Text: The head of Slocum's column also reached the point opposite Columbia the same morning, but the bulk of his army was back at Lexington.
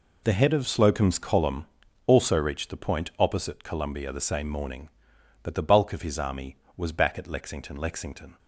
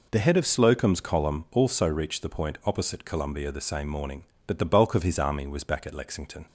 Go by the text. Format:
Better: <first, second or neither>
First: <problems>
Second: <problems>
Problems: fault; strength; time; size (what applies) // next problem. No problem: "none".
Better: second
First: pauses between "column" and "also"; at 1.6 s; 0.40 s long // says "Lexington" twice; at 7.7 s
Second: none